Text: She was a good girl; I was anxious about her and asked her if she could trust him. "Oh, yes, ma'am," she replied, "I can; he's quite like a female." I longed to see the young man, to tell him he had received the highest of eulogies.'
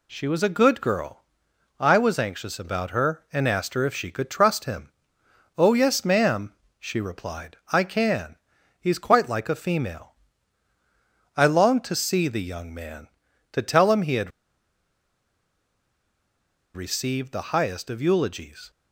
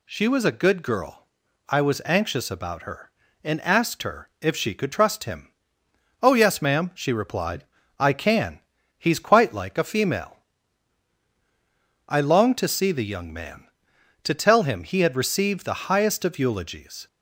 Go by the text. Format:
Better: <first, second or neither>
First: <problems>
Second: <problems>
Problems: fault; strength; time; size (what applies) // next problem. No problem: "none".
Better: second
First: pauses between "had" and "received"; strong; at 14.3 s; 2.4 s long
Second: none